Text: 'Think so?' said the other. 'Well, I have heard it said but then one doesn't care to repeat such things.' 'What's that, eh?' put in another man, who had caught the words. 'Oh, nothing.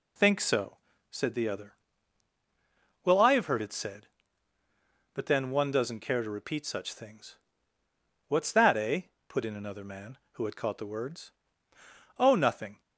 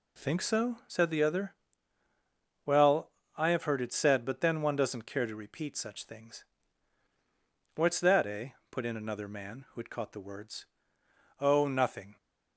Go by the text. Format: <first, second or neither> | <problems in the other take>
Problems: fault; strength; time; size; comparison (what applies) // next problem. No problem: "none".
neither | none